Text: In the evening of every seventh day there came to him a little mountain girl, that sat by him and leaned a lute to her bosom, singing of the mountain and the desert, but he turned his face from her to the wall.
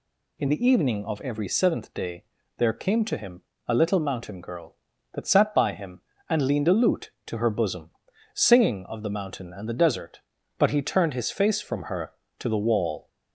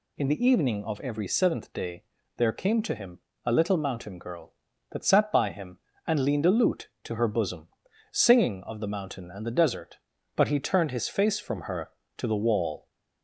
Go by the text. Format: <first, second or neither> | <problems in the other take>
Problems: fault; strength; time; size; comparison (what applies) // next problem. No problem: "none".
neither | pauses between "day" and "there"; slight; the same in both // pauses between "him" and "a"; slight; the same in both